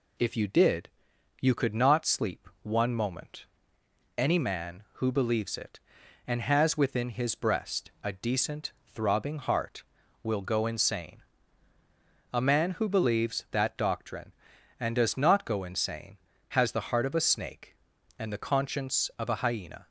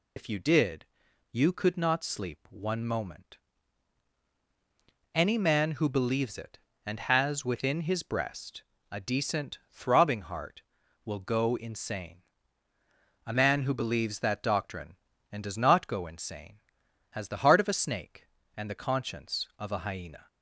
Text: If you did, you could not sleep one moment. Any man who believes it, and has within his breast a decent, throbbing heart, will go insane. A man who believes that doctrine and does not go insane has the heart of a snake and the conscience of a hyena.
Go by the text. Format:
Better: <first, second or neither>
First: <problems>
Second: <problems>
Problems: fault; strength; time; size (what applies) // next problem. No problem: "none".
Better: first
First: none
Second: loses the start of "If"; at 0.1 s; 95 ms // pauses between "breast" and "a"; slight; at 8.6 s; 0.28 s long